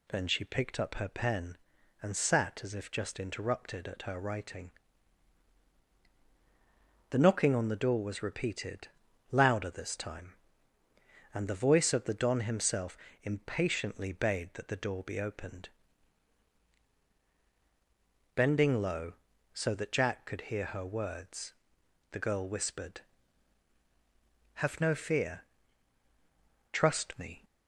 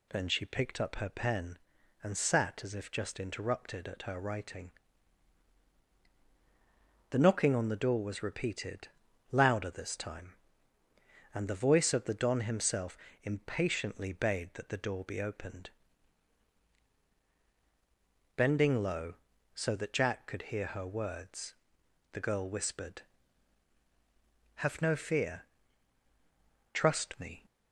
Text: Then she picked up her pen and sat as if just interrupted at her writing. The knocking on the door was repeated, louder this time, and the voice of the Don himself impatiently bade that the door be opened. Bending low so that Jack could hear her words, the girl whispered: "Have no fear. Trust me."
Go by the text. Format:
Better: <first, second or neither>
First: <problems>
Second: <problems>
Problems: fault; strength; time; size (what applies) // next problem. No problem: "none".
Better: neither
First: pauses between "himself" and "impatiently"; slight; at 12.9 s; 0.26 s long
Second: pauses between "himself" and "impatiently"; slight; at 12.9 s; 0.26 s long